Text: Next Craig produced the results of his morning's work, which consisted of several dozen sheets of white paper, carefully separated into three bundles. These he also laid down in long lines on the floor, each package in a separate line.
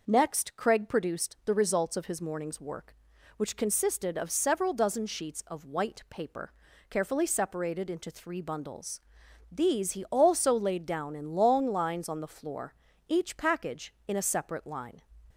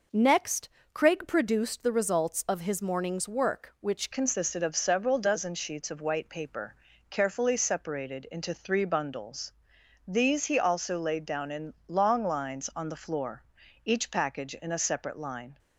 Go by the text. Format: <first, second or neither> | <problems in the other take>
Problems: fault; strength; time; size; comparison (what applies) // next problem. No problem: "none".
first | pauses between "Next" and "Craig"; slight; at 0.6 s; 0.22 s long // changes voice at "consisted"; from 4.1 s on; 11.4 s long